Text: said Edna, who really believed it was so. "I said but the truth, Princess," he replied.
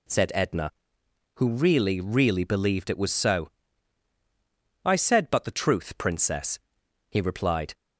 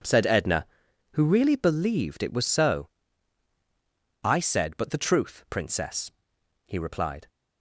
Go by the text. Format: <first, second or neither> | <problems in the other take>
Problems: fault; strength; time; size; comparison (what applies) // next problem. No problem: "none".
second | says "really" twice; at 1.9 s